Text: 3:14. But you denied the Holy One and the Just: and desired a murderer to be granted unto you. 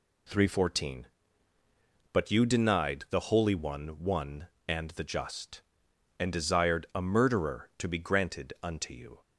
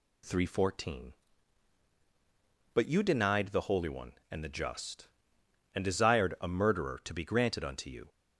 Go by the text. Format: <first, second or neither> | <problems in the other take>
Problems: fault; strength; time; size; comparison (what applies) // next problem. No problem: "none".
second | says "One" twice; at 4.0 s